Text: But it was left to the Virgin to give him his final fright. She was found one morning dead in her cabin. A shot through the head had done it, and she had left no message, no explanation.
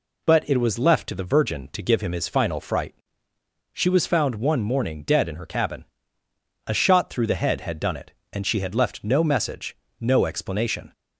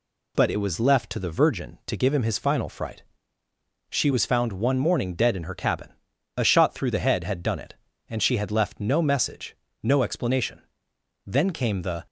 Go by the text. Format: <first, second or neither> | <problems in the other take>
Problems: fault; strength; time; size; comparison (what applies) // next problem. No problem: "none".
first | goes on to say "Then came the"; noticeable; from 11.2 s on; 0.80 s long